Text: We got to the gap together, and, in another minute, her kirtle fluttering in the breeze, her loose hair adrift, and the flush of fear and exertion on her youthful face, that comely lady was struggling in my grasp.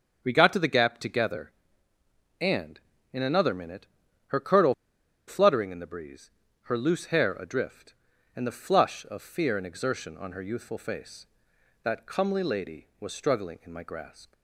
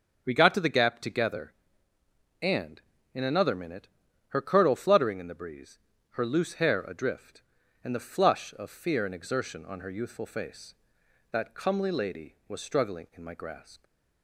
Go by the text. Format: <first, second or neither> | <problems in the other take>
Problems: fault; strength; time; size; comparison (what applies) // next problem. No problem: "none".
second | starts louder than the rest; until 1.2 s; 6 dB; also in the second // pauses between "kirtle" and "fluttering"; noticeable; at 4.7 s; 0.53 s long